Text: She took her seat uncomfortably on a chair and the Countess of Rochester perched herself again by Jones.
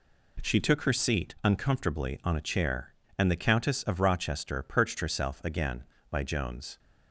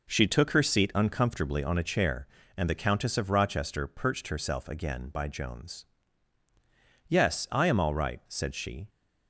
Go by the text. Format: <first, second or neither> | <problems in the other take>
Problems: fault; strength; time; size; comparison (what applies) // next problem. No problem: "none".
first | goes on to say "Yes I am all right said she"; strong; from 7.0 s on; 1.8 s long